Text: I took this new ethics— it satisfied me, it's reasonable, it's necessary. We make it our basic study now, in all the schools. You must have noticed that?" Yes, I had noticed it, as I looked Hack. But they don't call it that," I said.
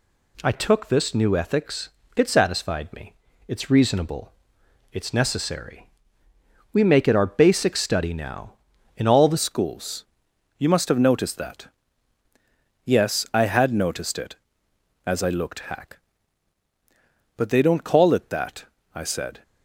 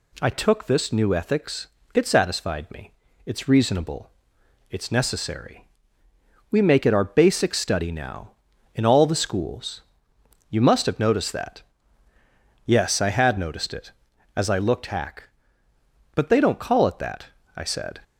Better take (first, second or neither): second